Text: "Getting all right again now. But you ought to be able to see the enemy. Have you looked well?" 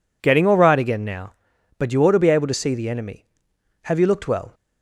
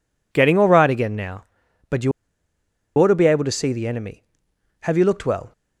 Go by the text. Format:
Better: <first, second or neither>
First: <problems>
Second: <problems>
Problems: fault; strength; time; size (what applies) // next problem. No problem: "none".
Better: first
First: none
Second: pauses between "you" and "ought"; noticeable; at 2.1 s; 0.86 s long